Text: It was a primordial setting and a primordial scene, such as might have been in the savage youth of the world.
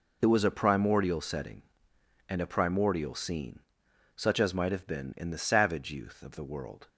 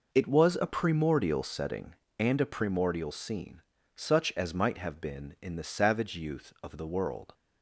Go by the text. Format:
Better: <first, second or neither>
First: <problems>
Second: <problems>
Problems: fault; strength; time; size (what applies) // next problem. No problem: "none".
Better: neither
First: none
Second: none